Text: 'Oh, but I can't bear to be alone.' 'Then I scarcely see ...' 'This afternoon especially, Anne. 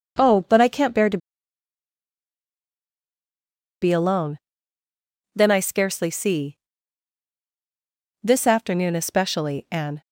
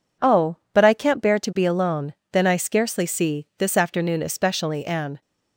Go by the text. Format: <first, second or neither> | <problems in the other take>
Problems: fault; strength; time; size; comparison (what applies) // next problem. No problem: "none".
second | starts louder than the rest; until 3.8 s; 6.5 dB // pauses between "to" and "be"; strong; at 1.1 s; 2.6 s long